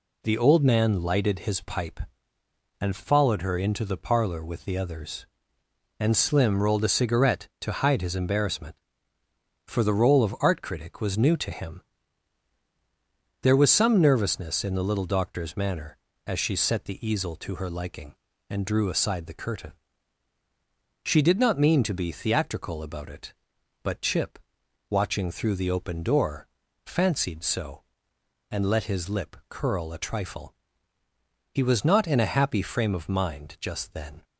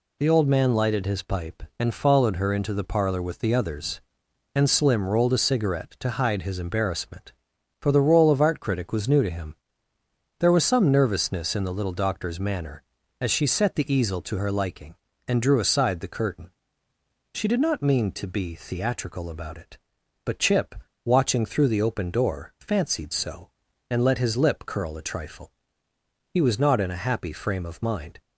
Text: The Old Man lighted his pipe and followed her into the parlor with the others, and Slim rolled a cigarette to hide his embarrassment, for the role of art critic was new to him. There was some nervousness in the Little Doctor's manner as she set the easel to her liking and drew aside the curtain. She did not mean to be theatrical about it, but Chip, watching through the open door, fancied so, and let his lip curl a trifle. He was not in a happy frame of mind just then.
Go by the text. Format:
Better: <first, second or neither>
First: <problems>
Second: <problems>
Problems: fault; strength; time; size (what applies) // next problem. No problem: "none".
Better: first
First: none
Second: stops before "just then"; at 28.2 s